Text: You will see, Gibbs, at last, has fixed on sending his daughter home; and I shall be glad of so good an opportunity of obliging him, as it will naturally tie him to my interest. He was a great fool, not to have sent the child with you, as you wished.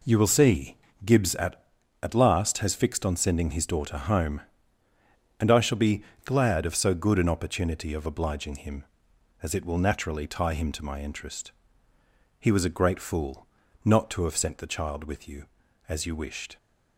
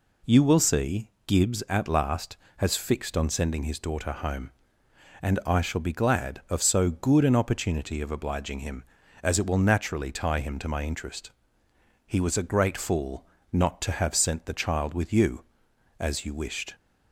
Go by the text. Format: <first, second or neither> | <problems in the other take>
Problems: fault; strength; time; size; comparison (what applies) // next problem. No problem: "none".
second | says "at" twice; at 2.0 s // pauses between "be" and "glad"; slight; at 6.0 s; 0.22 s long